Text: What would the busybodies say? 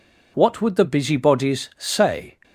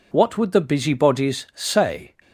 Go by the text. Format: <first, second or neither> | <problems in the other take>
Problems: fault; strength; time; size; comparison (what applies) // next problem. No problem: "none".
neither | none